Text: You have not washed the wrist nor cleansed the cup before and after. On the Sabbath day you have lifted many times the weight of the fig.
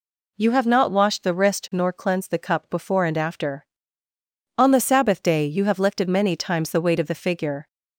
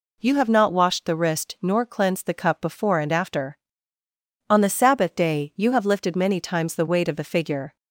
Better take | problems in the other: neither | none

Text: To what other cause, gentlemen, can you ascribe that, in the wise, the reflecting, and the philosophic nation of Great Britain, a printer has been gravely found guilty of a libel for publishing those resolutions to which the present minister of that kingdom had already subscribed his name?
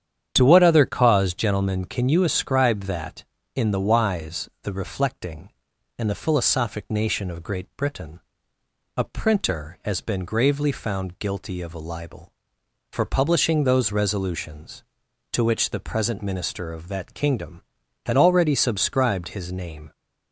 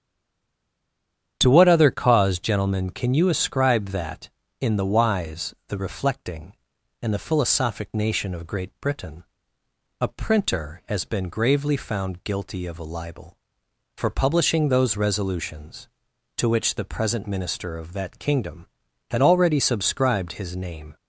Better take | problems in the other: first | stays silent before the first word; noticeable; until 1.3 s; 1.3 s long // starts louder than the rest; strong; until 2.4 s; 9 dB; strong in the first

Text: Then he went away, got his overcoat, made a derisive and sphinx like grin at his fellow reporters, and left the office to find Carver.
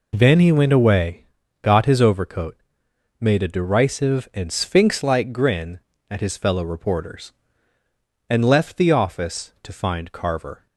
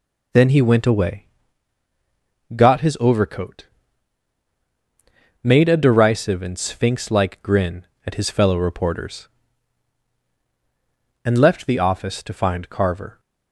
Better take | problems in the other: neither | none

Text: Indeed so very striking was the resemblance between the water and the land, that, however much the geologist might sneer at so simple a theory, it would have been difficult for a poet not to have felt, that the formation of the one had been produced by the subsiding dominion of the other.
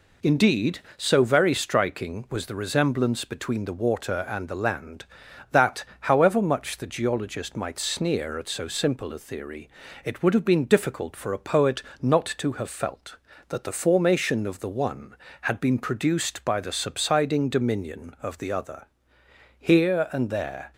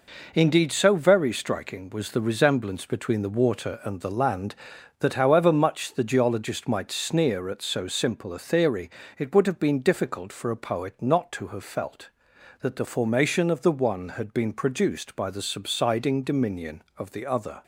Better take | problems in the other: second | pauses between "poet" and "not"; slight; at 11.8 s; 0.20 s long // goes on to say "Here and there"; noticeable; from 19.5 s on; 1.1 s long

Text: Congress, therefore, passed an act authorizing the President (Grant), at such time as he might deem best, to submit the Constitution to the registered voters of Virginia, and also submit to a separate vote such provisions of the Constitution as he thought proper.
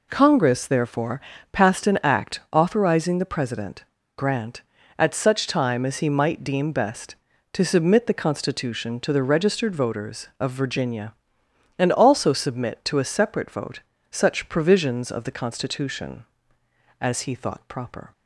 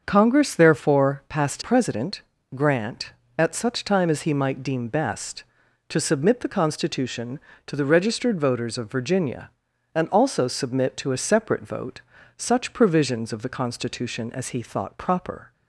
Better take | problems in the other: first | starts louder than the rest; until 1.0 s; 7 dB // skips "an act authorizing the"; at 1.6 s // pauses between "vote" and "such"; slight; at 12.0 s; 0.36 s long; slight in the first

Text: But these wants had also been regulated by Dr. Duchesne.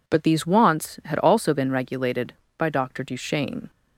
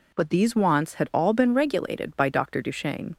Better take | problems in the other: first | says "all" for "also"; at 1.1 s

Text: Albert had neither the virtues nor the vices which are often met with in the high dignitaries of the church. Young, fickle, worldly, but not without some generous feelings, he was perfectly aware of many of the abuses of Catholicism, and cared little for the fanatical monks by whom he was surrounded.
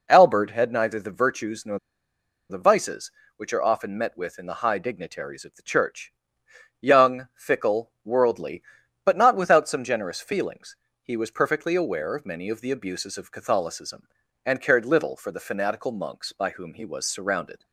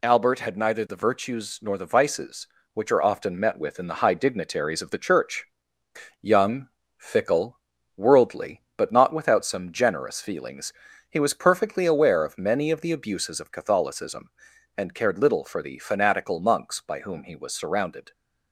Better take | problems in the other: second | pauses between "nor" and "the"; noticeable; at 1.7 s; 0.70 s long

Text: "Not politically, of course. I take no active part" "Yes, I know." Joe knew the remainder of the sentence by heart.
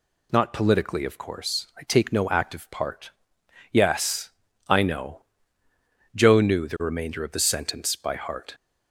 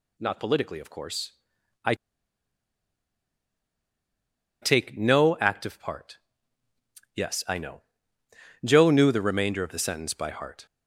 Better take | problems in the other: first | pauses between "I" and "take"; strong; at 1.9 s; 2.6 s long // pauses between "part" and "Yes"; noticeable; at 6.1 s; 0.96 s long; noticeable in the first

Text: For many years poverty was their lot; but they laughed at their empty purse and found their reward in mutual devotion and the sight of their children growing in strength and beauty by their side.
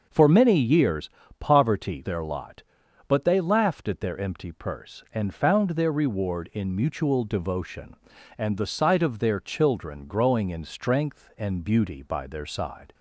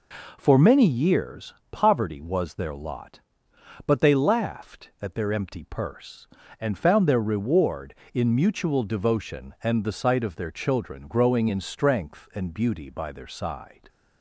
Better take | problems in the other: second | starts louder than the rest; noticeable; until 1.1 s; 6 dB // pauses between "years" and "poverty"; slight; at 1.1 s; 0.28 s long; slight in the second // skips "was"; at 2.0 s

